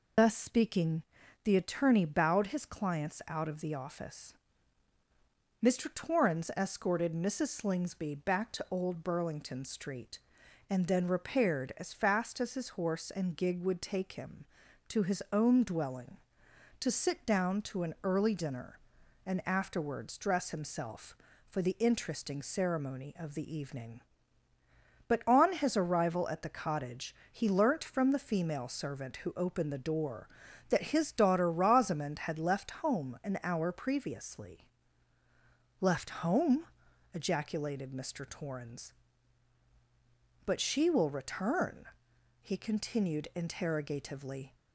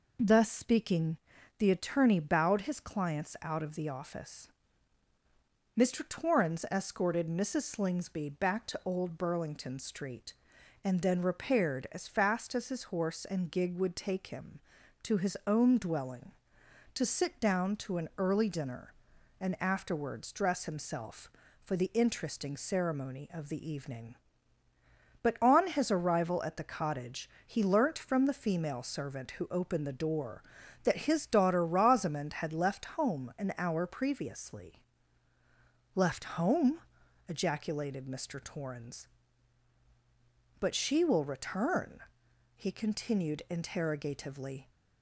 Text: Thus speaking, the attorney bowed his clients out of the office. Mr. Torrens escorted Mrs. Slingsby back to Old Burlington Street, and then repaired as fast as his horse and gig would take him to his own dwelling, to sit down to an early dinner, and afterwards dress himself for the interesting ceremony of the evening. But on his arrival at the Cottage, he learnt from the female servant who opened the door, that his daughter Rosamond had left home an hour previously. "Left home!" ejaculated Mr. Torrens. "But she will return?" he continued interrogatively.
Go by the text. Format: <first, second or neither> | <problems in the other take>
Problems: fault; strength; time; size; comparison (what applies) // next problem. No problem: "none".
second | loses the start of "Thus"; at 0.1 s; 130 ms